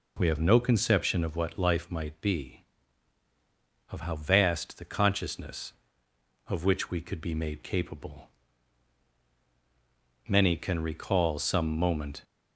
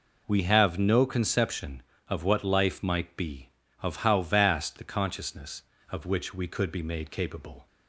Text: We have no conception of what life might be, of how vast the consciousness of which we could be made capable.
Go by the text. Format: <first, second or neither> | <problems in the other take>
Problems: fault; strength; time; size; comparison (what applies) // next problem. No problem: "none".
second | goes on to say "Many can recall some moment"; strong; from 10.2 s on; 1.9 s long